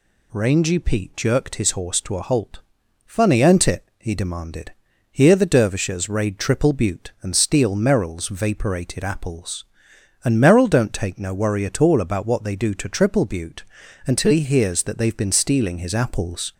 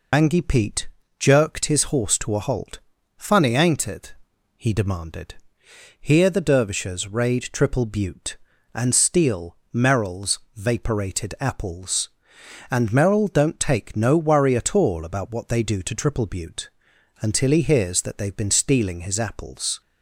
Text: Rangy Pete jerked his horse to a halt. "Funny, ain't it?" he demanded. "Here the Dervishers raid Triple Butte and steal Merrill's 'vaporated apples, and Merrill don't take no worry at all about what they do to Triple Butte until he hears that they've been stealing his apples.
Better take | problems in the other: first | loses the start of "Rangy"; at 0.1 s; 120 ms // pauses between "Pete" and "jerked"; slight; at 0.8 s; 0.32 s long // pauses between "steal" and "Merrill's"; slight; at 9.5 s; 0.16 s long // pauses between "Merrill's" and "vaporated"; slight; at 10.3 s; 0.16 s long // pauses between "Butte" and "until"; noticeable; at 16.6 s; 0.52 s long; also in the first

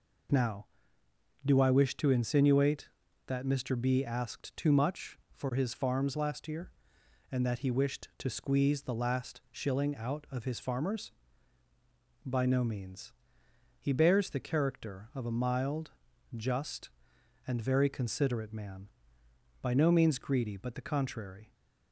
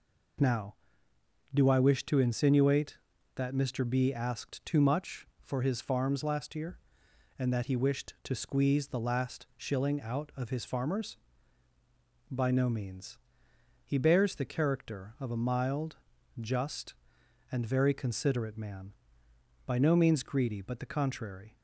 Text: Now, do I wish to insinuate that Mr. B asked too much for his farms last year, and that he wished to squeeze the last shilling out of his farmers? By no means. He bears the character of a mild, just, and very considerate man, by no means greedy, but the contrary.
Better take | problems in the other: neither | none

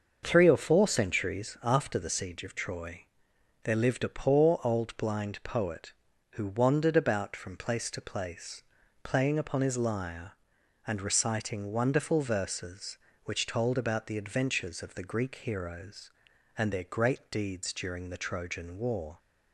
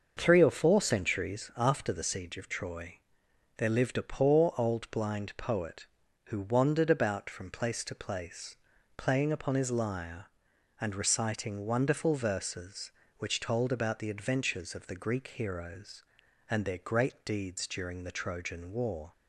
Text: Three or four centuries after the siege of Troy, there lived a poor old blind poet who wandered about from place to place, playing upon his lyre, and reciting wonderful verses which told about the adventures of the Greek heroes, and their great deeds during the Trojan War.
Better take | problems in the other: neither | starts louder than the rest; the same in both

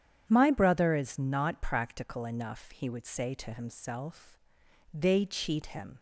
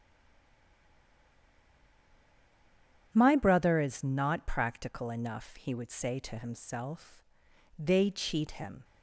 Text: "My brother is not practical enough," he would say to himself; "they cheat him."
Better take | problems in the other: first | stays silent before the first word; strong; until 3.1 s; 3.1 s long // starts louder than the rest; strong; until 4.1 s; 9 dB; strong in the first

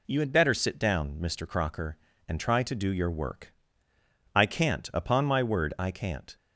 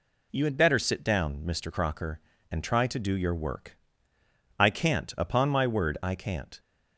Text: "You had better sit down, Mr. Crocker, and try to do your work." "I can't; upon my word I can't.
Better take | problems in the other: neither | none

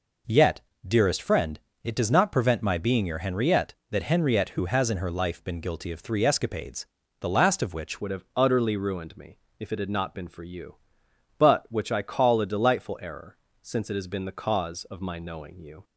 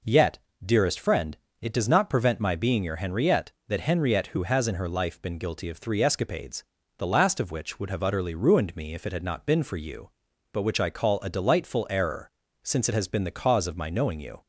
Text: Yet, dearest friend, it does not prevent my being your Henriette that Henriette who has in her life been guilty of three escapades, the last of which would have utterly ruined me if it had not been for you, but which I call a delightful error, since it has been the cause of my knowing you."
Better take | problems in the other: second | changes voice at "would"; from 8.0 s on; 7.8 s long // pauses between "me" and "if"; slight; at 9.3 s; 0.20 s long

